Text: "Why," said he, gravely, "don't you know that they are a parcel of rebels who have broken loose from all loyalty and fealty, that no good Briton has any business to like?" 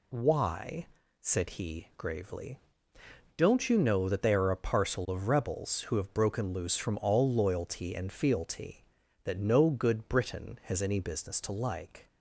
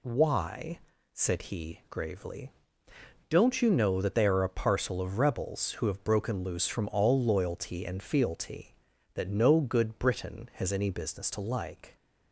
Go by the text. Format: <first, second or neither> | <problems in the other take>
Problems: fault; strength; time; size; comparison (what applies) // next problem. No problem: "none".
neither | none